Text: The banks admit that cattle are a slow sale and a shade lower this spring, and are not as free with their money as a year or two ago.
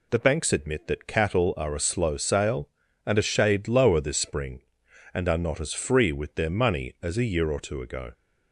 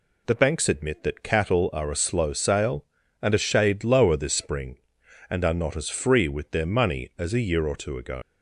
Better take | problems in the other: first | leaves "ago" unfinished; at 8.2 s; 70 ms

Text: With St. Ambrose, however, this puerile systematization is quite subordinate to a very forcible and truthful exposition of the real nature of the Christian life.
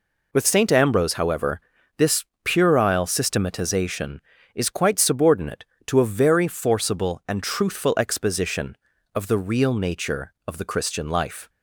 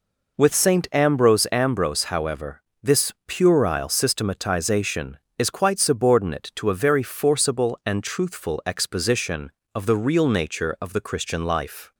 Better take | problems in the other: first | says "Ambrose" twice; at 1.5 s // pauses between "this" and "puerile"; slight; at 3.1 s; 0.16 s long; slight in the first

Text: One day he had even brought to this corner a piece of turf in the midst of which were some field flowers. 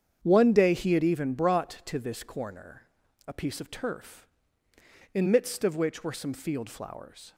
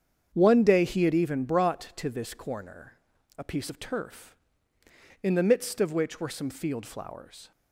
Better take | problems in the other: second | starts louder than the rest; strong; until 1.2 s; 8 dB; strong in the second // pauses between "corner" and "a"; at 2.8 s; 0.44 s long; also in the second // skips "the"; at 5.2 s

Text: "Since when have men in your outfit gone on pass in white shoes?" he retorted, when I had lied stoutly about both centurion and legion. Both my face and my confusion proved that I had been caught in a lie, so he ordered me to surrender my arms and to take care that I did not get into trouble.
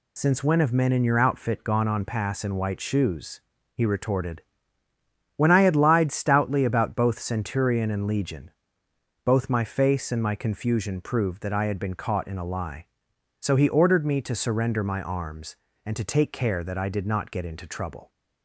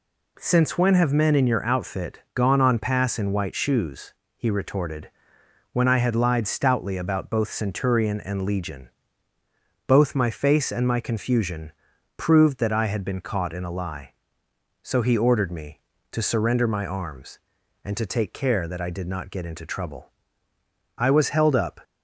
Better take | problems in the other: first | pauses between "confusion" and "proved"; at 11.7 s; 0.44 s long // goes on to say "I was held up"; noticeable; from 20.9 s on; 0.82 s long

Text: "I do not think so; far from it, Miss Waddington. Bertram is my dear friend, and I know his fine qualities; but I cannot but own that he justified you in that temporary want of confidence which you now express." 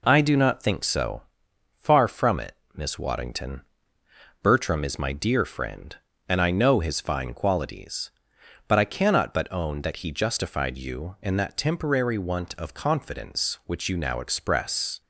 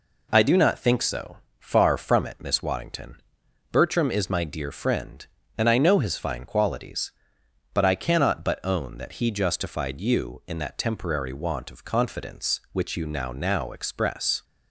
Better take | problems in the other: first | says "now" twice; at 13.3 s

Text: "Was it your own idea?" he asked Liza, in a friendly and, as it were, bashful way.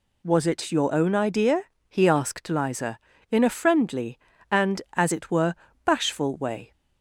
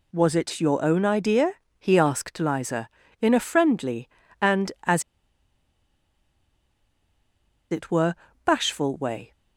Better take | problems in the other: first | pauses between "as" and "it"; strong; at 5.0 s; 2.6 s long

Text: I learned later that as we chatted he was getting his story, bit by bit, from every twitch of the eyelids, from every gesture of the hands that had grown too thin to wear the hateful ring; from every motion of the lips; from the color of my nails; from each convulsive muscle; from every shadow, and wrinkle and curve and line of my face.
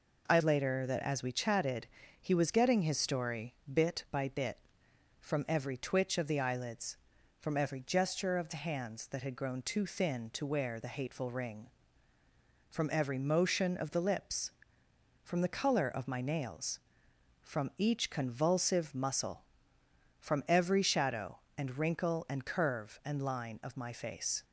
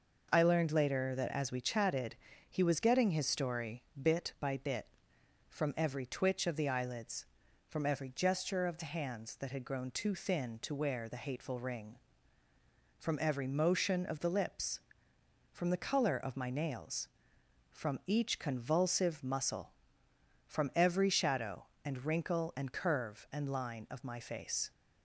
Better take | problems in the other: second | skips "learned"; at 0.4 s // pauses between "chatted" and "he"; slight; at 1.8 s; 0.32 s long; slight in the second

